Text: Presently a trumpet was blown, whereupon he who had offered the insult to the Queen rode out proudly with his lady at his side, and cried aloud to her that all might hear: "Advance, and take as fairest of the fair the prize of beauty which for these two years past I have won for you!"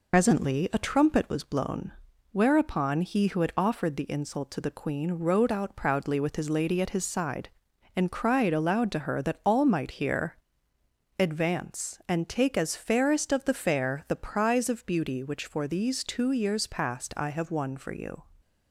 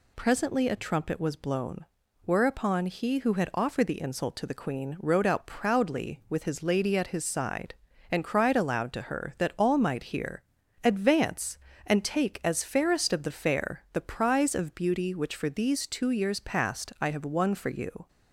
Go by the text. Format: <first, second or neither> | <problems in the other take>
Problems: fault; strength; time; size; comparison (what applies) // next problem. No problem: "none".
second | loses the start of "Presently"; at 0.1 s; 80 ms